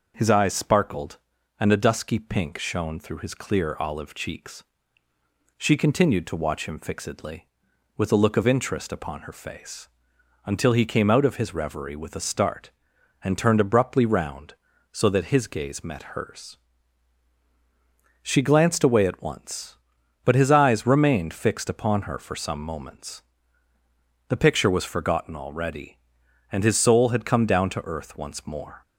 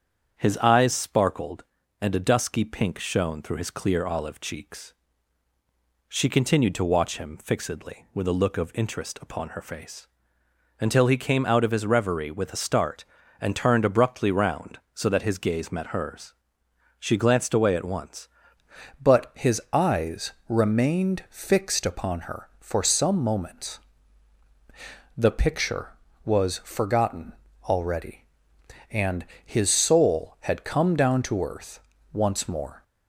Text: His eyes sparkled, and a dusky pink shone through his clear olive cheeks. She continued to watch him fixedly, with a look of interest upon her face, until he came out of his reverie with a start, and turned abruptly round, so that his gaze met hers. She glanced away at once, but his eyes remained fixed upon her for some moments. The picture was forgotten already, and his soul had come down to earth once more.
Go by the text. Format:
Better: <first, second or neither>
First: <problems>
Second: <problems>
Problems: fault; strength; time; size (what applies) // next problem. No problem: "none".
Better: first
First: none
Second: starts louder than the rest; strong; until 1.3 s; 8 dB // changes voice at "but"; from 19.0 s on; 13.8 s long // pauses between "eyes" and "remained"; slight; at 20.3 s; 0.16 s long // pauses between "forgotten" and "already"; slight; at 27.3 s; 0.32 s long // pauses between "and" and "his"; slight; at 29.2 s; 0.20 s long // pauses between "earth" and "once"; slight; at 31.7 s; 0.34 s long